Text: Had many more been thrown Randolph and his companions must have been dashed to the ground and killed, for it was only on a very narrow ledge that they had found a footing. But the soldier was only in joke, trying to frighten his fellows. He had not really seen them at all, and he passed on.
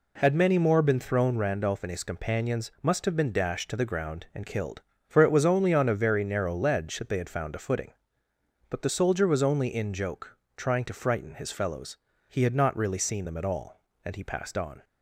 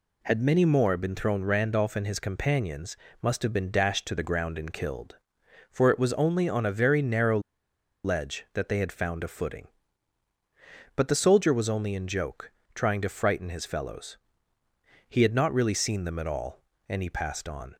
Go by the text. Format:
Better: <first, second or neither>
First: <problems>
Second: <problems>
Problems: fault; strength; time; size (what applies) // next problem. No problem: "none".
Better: first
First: none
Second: pauses between "companions" and "must"; slight; at 2.9 s; 0.24 s long // pauses between "narrow" and "ledge"; noticeable; at 7.3 s; 0.65 s long